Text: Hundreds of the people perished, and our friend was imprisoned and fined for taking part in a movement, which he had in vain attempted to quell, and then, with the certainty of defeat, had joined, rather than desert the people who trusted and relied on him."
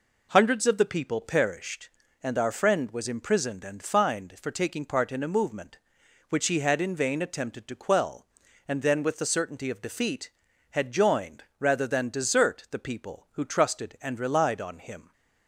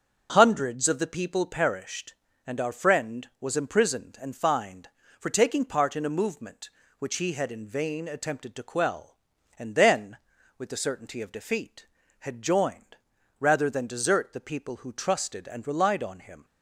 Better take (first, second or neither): neither